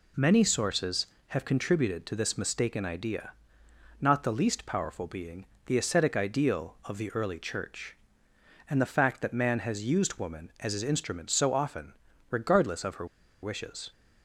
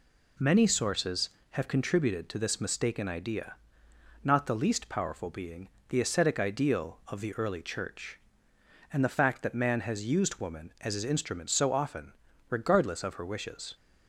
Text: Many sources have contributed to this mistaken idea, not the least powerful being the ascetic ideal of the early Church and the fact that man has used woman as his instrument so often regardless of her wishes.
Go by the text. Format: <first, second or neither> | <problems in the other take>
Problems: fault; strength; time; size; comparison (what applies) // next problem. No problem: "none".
second | pauses between "being" and "the"; slight; at 5.4 s; 0.20 s long; slight in the second // pauses between "often" and "regardless"; slight; at 11.9 s; 0.36 s long; slight in the second // pauses between "her" and "wishes"; at 13.0 s; 0.36 s long